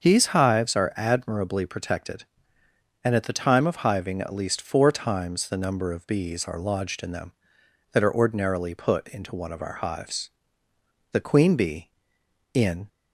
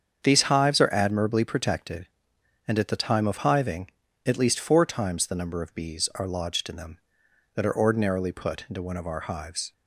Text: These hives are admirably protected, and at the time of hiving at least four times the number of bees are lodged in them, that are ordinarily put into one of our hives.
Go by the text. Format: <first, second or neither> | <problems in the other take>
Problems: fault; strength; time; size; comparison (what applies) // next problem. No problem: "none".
second | starts louder than the rest; until 1.0 s; 6.5 dB; strong in the second // goes on to say "The queen bee in"; strong; from 11.1 s on; 1.7 s long